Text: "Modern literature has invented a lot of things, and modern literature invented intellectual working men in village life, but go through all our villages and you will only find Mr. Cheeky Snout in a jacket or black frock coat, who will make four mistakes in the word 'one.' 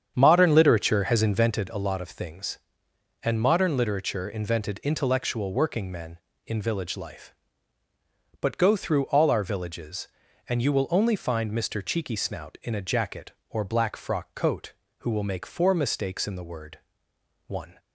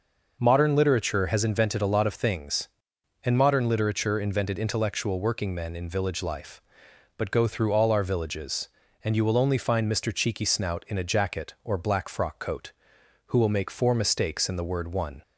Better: second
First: starts louder than the rest; strong; until 1.7 s; 8 dB // pauses between "word" and "one"; noticeable; at 16.7 s; 0.70 s long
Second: none

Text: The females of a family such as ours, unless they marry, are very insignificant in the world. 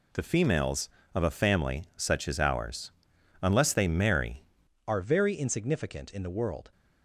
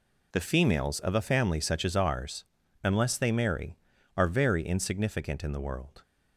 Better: second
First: changes voice at "are"; from 4.8 s on; 1.8 s long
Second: none

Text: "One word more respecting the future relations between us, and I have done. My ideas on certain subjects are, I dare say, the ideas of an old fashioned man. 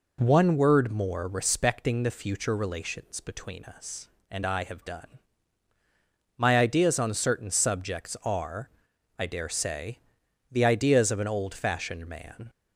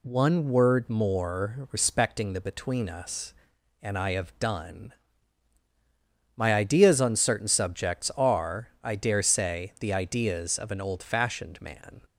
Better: first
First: none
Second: skips "future relations"; at 2.4 s

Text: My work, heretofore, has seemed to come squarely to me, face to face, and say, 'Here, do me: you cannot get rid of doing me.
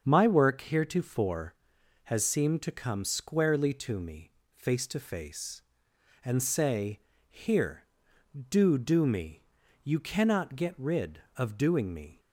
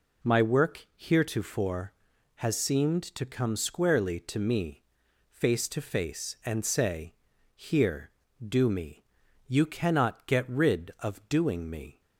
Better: second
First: starts louder than the rest; until 1.0 s; 7 dB // says "do" twice; at 8.7 s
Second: none

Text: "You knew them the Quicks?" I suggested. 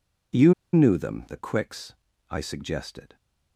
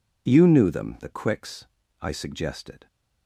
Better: second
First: pauses between "You" and "knew"; slight; at 0.5 s; 0.21 s long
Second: none

